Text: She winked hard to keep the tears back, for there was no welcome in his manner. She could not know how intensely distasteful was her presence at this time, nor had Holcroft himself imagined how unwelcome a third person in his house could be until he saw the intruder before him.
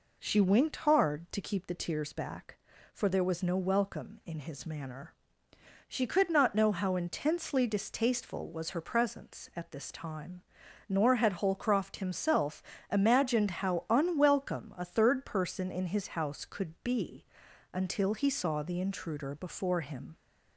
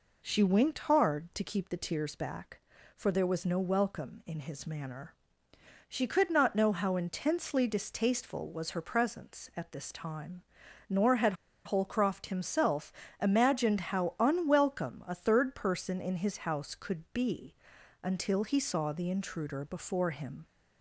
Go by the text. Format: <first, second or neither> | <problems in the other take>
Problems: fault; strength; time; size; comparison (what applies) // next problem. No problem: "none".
first | pauses between "had" and "Holcroft"; slight; at 11.3 s; 0.32 s long // pauses between "himself" and "imagined"; slight; at 12.9 s; 0.26 s long; slight in the first // pauses between "be" and "until"; noticeable; at 17.5 s; 0.48 s long; noticeable in the first